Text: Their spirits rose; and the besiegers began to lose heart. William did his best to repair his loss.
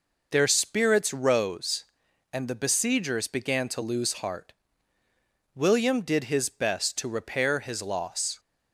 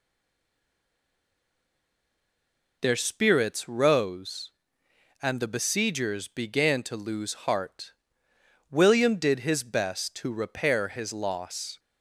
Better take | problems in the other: first | stays silent before the first word; strong; until 2.8 s; 2.8 s long

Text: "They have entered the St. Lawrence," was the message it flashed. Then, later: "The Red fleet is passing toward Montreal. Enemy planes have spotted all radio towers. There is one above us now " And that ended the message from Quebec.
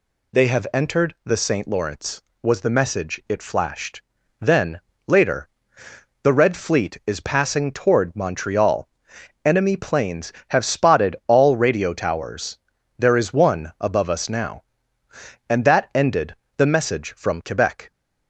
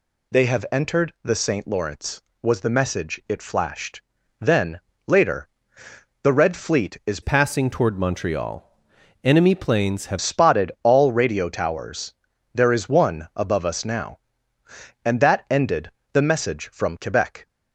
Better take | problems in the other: first | changes voice from "passing" to "have"; from 7.2 to 10.2 s; 3.0 s long // pauses between "ended" and "the"; slight; at 15.8 s; 0.22 s long; slight in the first

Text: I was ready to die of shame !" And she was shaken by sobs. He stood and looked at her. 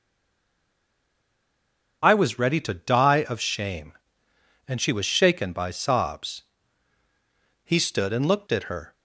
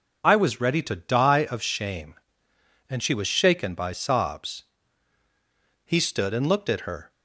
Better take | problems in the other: second | stays silent before the first word; noticeable; until 2.0 s; 2.0 s long

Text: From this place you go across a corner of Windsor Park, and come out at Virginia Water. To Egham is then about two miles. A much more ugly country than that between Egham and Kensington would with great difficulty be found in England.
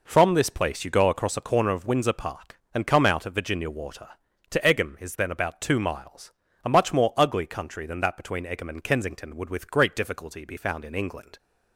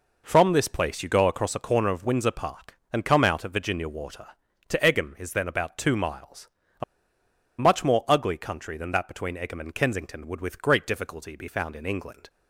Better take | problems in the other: first | pauses between "A" and "much"; noticeable; at 6.8 s; 0.77 s long

